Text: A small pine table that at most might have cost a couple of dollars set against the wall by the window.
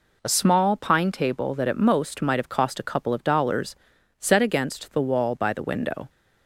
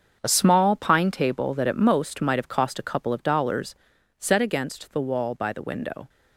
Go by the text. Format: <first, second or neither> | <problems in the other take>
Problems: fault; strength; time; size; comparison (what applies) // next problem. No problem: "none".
first | gets quieter; strong; throughout; 11.5 dB // pauses between "dollars" and "set"; at 3.7 s; 0.44 s long; also in the first